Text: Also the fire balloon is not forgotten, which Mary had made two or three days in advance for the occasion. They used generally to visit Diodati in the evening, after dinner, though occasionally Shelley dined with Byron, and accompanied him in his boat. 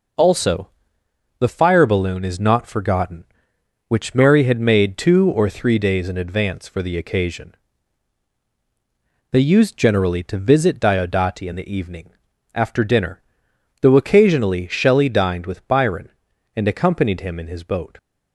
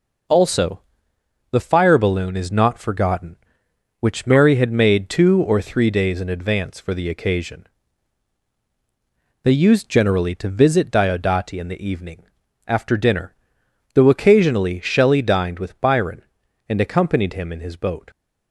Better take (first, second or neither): neither